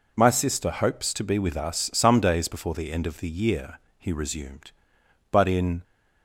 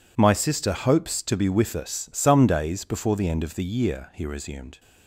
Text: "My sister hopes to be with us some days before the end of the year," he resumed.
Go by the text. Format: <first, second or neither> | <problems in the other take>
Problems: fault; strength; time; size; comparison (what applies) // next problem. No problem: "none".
second | goes on to say "But in"; from 5.2 s on; 0.54 s long